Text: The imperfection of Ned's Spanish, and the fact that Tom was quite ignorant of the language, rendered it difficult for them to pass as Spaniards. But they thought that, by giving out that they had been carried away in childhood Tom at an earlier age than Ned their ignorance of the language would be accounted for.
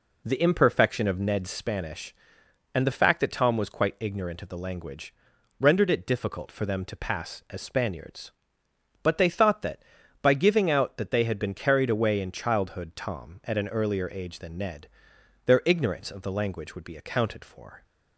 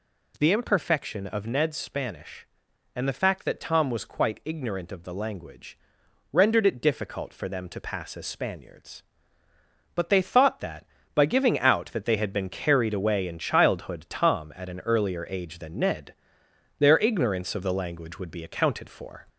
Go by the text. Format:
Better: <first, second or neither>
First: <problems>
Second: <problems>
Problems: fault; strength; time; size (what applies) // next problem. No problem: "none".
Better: first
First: pauses between "Ned" and "their"; noticeable; at 14.8 s; 0.58 s long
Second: gets louder; slight; throughout; 2 dB // pauses between "Ned" and "their"; noticeable; at 16.1 s; 0.64 s long